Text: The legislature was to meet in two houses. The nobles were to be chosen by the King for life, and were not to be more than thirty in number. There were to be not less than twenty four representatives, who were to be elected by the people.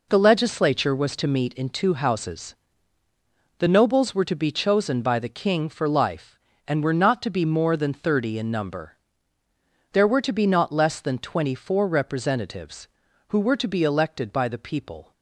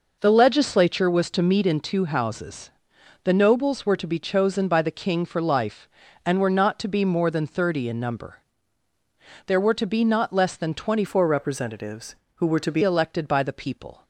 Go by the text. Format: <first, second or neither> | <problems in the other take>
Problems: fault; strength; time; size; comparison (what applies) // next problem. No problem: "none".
first | changes voice from "four" to "be"; from 11.0 to 12.8 s; 1.8 s long